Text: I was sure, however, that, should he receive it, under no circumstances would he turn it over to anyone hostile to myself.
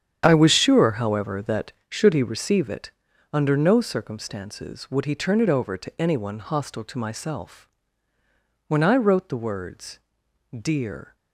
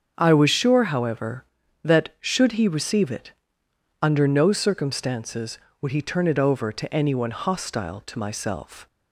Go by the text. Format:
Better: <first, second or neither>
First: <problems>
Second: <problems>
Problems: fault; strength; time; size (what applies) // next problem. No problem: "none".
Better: second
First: starts louder than the rest; strong; until 1.2 s; 9 dB // goes on to say "When I wrote the words Dear"; strong; from 8.6 s on; 2.4 s long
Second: starts louder than the rest; until 1.1 s; 7 dB